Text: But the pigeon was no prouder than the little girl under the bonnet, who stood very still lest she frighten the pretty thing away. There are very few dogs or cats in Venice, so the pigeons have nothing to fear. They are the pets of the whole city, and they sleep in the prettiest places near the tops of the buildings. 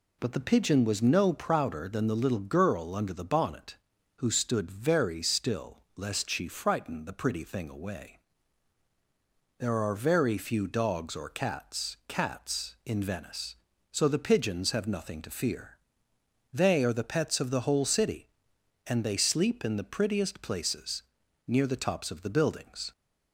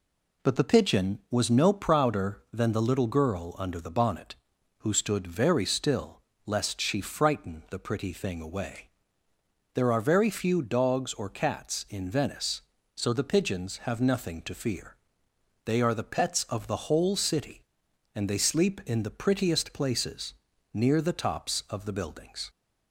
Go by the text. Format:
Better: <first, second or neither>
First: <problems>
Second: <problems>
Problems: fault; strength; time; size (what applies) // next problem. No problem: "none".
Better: second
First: pauses between "still" and "lest"; slight; at 5.7 s; 0.18 s long // says "cats" twice; at 12.0 s // pauses between "places" and "near"; noticeable; at 21.0 s; 0.46 s long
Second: pauses between "still" and "lest"; slight; at 6.2 s; 0.24 s long // pauses between "places" and "near"; at 20.3 s; 0.40 s long